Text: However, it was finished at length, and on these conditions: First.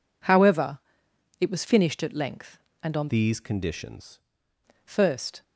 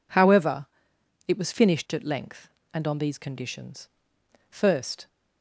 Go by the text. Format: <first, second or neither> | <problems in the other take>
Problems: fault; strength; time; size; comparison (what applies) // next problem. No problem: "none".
second | changes voice from "these" to "conditions"; from 3.1 to 4.2 s; 1.1 s long